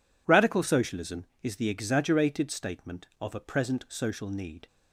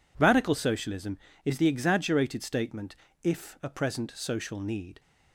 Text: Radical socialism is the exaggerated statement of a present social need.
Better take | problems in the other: first | says "if" for "of"; at 3.2 s

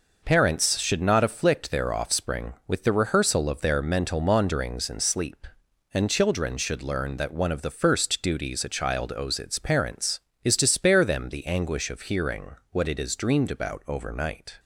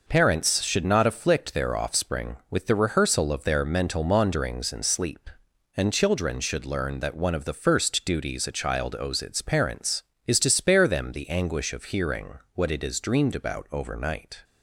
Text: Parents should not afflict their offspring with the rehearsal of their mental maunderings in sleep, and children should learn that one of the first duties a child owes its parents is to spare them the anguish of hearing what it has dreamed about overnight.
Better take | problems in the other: neither | pauses between "hearing" and "what"; slight; the same in both

